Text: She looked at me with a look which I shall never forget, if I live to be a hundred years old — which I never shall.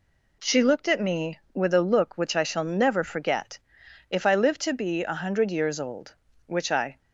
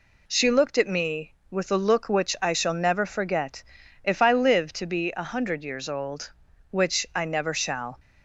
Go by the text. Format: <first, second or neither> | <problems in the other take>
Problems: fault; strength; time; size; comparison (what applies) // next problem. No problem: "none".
second | stops before "never shall"; at 6.9 s